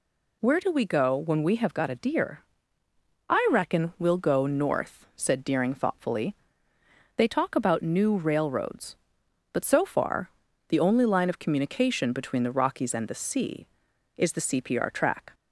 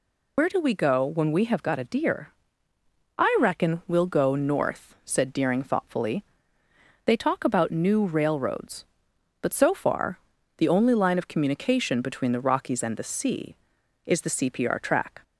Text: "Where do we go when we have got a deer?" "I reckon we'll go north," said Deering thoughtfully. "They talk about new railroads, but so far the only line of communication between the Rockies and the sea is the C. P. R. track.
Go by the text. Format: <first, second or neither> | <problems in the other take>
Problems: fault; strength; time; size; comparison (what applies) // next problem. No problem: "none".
first | loses the start of "Where"; at 0.3 s; 95 ms // pauses between "far" and "the"; at 10.1 s; 0.40 s long; also in the first